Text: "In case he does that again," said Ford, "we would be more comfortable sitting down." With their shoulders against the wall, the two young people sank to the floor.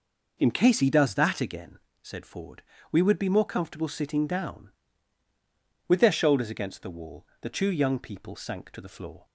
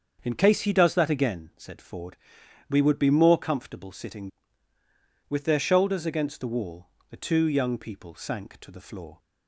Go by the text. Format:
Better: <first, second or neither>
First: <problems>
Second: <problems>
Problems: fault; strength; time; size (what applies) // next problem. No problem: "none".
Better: first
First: none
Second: starts louder than the rest; until 1.2 s; 7 dB // skips "down"; at 4.7 s